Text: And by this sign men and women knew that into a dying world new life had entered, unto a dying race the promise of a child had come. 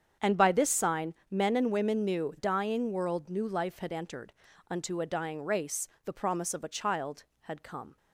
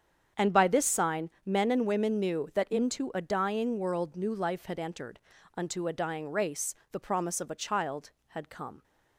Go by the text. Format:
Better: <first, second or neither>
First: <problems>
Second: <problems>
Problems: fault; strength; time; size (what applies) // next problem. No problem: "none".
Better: second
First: starts louder than the rest; strong; until 1.3 s; 8 dB // pauses between "sign" and "men"; slight; at 1.1 s; 0.16 s long // skips "that into a"; at 2.3 s // pauses between "race" and "the"; slight; at 5.8 s; 0.16 s long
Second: starts louder than the rest; strong; until 1.5 s; 8 dB // pauses between "sign" and "men"; slight; at 1.2 s; 0.15 s long // pauses between "race" and "the"; slight; at 6.7 s; 0.16 s long